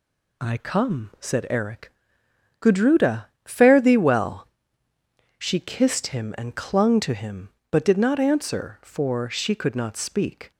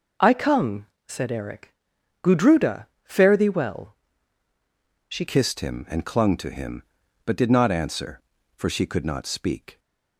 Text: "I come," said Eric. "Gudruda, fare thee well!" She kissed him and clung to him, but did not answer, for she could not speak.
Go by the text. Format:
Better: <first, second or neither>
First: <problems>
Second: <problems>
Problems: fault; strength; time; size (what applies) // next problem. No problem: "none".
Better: first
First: none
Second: changes voice at "kissed"; from 5.2 s on; 4.5 s long